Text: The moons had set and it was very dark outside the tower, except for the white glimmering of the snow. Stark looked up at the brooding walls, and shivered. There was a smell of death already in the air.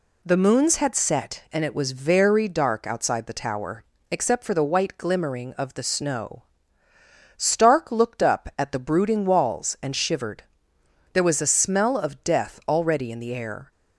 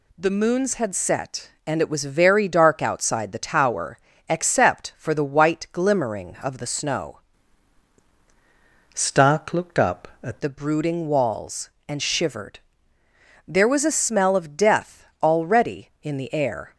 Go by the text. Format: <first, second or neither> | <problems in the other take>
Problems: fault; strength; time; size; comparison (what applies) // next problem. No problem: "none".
first | changes voice from "Stark" to "at"; from 8.9 to 10.4 s; 1.5 s long // pauses between "death" and "already"; slight; at 15.0 s; 0.18 s long